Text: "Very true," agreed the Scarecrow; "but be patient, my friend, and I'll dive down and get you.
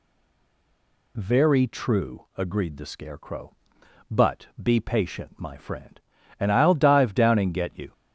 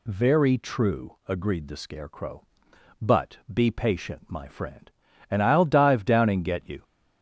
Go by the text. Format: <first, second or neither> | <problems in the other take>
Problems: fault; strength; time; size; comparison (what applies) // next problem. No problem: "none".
second | stays silent before the first word; until 1.1 s; 1.1 s long